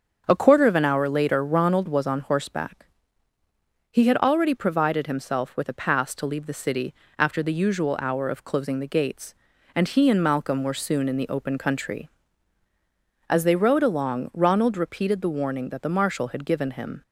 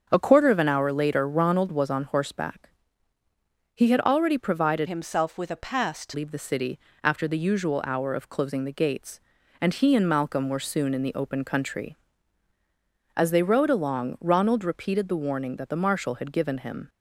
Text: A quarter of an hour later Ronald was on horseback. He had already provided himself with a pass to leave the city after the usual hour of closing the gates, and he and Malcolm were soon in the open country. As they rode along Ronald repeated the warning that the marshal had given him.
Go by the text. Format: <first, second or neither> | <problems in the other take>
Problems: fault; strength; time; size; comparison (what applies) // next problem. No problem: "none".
first | starts louder than the rest; until 1.1 s; 7 dB; also in the first // changes voice from "himself" to "to"; from 4.8 to 6.1 s; 1.3 s long // pauses between "city" and "after"; slight; at 6.7 s; 0.24 s long; slight in the first